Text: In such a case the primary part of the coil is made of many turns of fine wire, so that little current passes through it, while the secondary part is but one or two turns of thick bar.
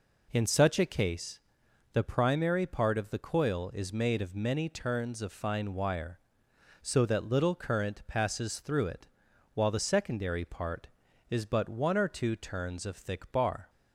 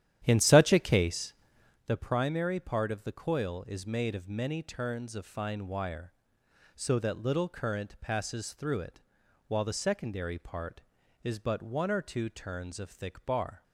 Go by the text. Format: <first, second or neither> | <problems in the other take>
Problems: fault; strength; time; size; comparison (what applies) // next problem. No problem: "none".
first | starts louder than the rest; strong; until 1.8 s; 11 dB // pauses between "case" and "the"; noticeable; at 1.3 s; 0.54 s long; noticeable in the first